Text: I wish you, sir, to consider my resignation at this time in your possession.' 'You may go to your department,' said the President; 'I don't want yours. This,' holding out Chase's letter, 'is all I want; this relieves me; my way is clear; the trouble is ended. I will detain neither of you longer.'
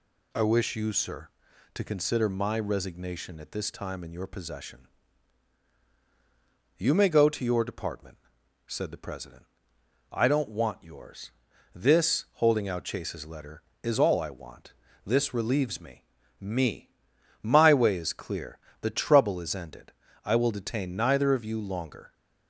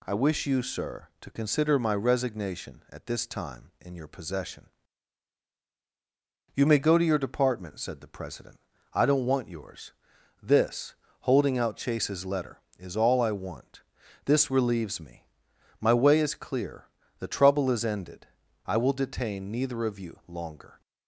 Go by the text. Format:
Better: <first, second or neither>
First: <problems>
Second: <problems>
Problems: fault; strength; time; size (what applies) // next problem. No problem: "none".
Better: second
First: says "me" twice; at 16.3 s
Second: none